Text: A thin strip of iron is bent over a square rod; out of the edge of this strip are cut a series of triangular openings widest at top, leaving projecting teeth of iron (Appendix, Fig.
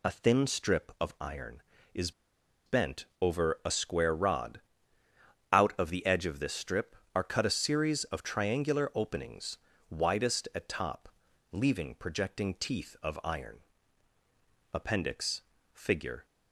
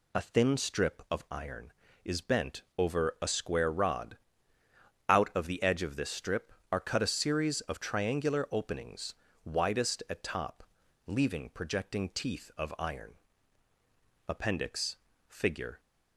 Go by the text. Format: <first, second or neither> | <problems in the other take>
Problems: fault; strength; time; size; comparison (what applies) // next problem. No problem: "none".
second | pauses between "is" and "bent"; noticeable; at 2.1 s; 0.55 s long // pauses between "bent" and "over"; slight; at 3.0 s; 0.16 s long; slight in the second // pauses between "openings" and "widest"; slight; at 9.5 s; 0.32 s long; slight in the second